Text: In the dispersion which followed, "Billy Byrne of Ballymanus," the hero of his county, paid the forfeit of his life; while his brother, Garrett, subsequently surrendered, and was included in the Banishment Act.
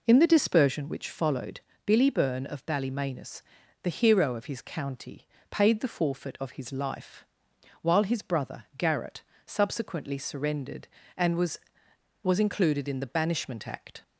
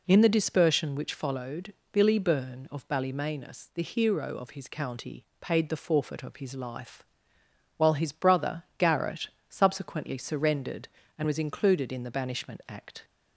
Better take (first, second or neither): second